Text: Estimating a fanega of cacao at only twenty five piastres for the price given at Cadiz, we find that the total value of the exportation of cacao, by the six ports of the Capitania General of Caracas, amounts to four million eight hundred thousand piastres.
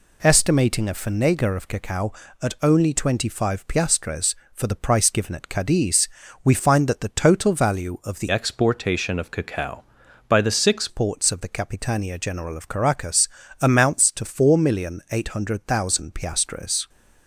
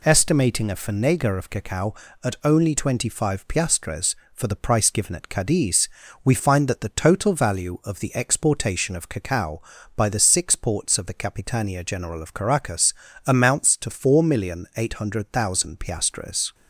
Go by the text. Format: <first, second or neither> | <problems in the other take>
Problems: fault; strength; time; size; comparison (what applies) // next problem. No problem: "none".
second | changes voice from "exportation" to "six"; from 8.2 to 10.8 s; 2.6 s long